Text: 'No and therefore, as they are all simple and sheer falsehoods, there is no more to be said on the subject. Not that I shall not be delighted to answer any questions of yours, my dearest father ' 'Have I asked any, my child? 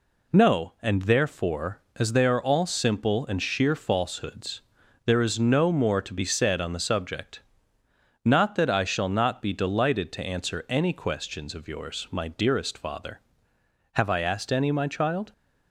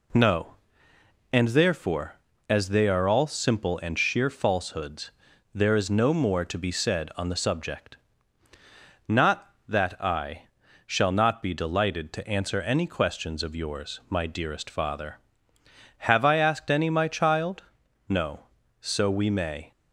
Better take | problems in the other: first | pauses between "I" and "shall"; at 10.4 s; 0.38 s long // goes on to say "No So we may"; from 18.0 s on; 1.6 s long

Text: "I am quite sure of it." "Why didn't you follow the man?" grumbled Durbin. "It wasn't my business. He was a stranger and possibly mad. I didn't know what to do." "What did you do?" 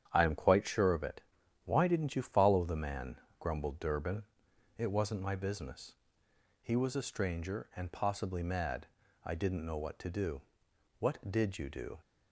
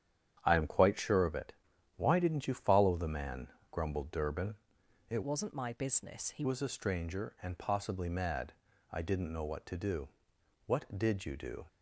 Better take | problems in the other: first | starts louder than the rest; strong; until 1.4 s; 9.5 dB; strong in the first // changes voice from "wasn't" to "He"; from 5.2 to 6.4 s; 1.2 s long

